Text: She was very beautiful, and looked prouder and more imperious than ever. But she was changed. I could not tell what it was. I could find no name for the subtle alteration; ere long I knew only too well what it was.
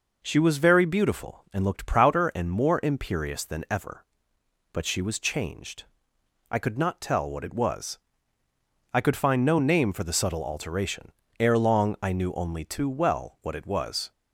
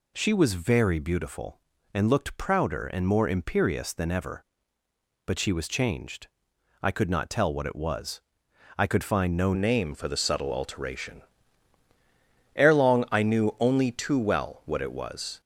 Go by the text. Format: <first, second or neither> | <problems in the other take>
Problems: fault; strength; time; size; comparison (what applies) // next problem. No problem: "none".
first | changes voice at "name"; from 9.5 s on; 5.9 s long